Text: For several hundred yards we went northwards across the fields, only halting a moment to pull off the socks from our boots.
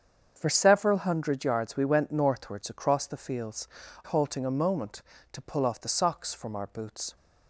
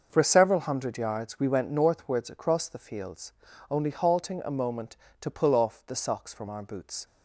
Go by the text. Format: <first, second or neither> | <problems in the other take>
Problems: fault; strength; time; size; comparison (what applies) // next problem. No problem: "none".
second | starts louder than the rest; strong; until 1.3 s; 7.5 dB; also in the second // skips "only"; at 3.8 s